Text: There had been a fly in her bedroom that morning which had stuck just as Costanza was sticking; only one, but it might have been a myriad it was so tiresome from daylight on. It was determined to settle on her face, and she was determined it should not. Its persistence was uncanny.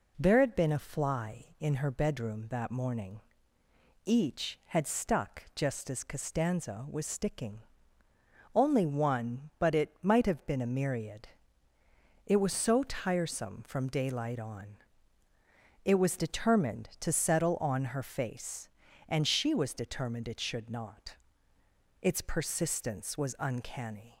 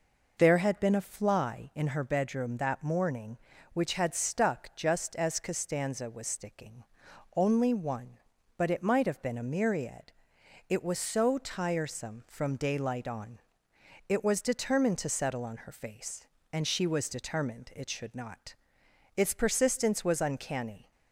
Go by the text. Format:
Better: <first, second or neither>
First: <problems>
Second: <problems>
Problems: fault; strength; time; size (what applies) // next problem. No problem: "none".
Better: second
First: says "each" for "which"; at 4.0 s // pauses between "myriad" and "it"; noticeable; at 11.2 s; 0.98 s long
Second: pauses between "myriad" and "it"; noticeable; at 10.1 s; 0.58 s long